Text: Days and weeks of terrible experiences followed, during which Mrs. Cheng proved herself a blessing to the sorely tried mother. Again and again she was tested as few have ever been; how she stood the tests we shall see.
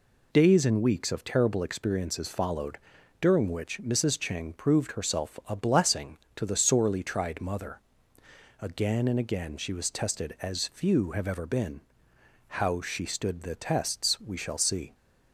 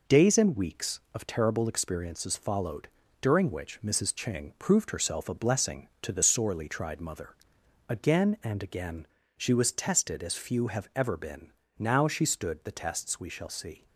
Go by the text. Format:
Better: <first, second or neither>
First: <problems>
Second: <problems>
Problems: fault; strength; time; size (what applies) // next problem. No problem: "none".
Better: first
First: none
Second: pauses between "again" and "she"; slight; at 9.0 s; 0.32 s long // says "now" for "how"; at 11.7 s